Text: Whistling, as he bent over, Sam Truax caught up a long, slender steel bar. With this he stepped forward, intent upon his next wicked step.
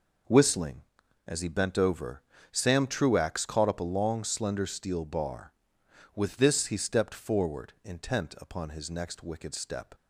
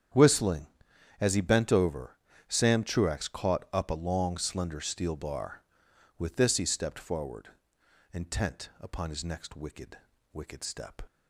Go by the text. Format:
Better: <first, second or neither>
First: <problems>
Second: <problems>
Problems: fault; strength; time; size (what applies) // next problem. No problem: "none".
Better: first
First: none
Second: starts louder than the rest; strong; until 1.7 s; 8.5 dB // says "wicked" twice; at 10.3 s